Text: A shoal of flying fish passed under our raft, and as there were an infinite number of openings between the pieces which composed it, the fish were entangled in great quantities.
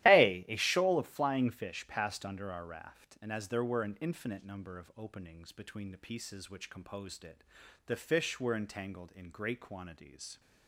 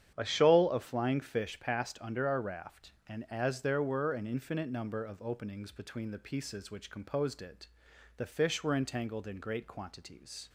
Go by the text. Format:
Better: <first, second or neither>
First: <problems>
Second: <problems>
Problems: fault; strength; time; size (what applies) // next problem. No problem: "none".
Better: second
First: starts louder than the rest; strong; until 1.1 s; 14.5 dB // says "A" twice; at 0.4 s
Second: starts louder than the rest; strong; until 1.1 s; 9 dB